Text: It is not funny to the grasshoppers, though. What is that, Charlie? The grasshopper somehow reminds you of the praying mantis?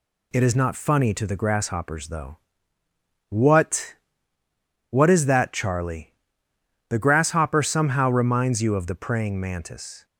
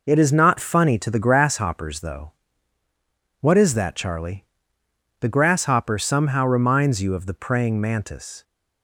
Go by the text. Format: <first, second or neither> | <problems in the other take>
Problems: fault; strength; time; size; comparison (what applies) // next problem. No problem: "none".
second | says "What" twice; at 4.8 s